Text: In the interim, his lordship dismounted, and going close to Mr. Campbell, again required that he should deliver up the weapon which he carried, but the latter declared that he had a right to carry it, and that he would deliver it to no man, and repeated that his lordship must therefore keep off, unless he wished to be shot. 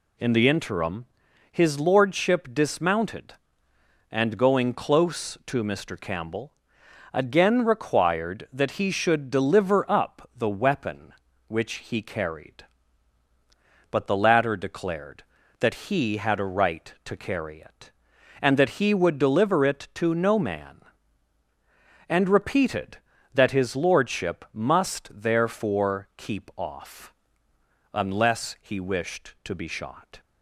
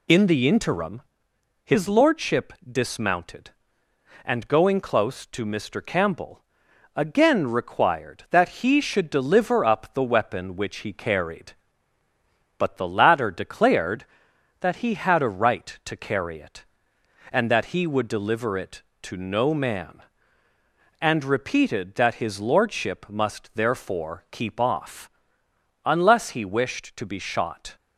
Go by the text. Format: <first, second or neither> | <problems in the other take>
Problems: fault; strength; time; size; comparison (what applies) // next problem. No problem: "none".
first | loses the start of "In"; at 0.0 s; 20 ms